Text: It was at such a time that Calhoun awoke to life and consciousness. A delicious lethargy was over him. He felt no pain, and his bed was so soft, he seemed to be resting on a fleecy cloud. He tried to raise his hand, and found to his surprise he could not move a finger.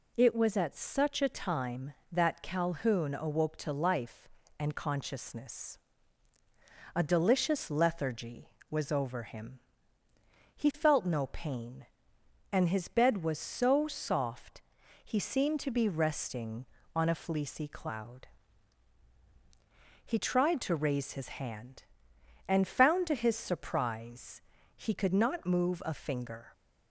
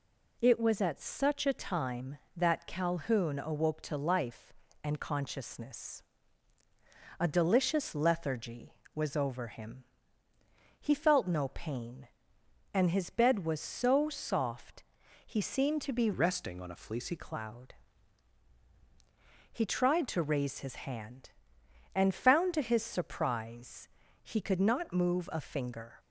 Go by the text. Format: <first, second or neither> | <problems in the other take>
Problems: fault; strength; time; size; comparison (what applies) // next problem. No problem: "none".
first | changes voice from "resting" to "fleecy"; from 16.1 to 17.1 s; 1.0 s long // pauses between "surprise" and "he"; at 23.8 s; 0.38 s long; also in the first